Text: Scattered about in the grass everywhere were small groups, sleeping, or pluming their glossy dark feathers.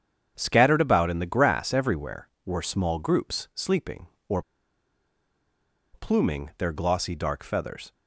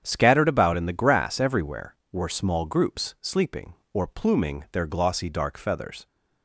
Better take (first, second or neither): second